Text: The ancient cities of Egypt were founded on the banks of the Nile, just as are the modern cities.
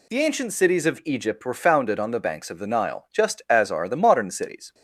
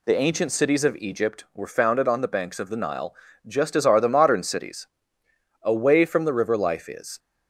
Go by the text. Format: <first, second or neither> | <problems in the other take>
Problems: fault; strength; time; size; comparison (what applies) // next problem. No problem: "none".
first | goes on to say "Away from the river life is"; from 5.6 s on; 1.5 s long